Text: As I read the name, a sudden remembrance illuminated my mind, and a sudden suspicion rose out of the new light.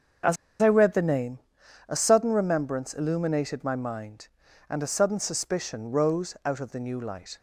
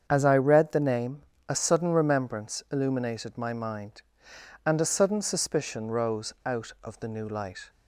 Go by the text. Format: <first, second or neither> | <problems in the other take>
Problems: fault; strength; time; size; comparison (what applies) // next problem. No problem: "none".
second | starts louder than the rest; until 2.0 s; 6.5 dB; strong in the second // pauses between "As" and "I"; slight; at 0.3 s; 0.26 s long